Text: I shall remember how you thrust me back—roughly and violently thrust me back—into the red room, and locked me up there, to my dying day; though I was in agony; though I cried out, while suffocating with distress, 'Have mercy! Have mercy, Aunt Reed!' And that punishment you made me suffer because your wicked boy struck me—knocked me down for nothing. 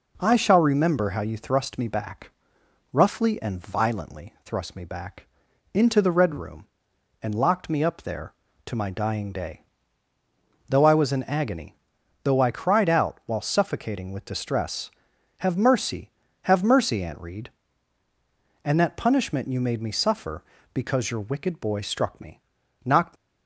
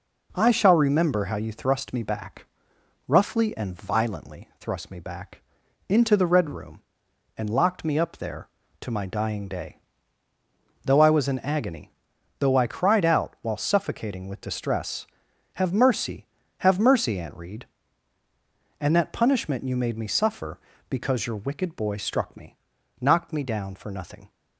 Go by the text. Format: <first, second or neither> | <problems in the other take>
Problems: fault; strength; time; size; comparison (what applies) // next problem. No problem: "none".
second | stops before "me down for nothing"; at 23.1 s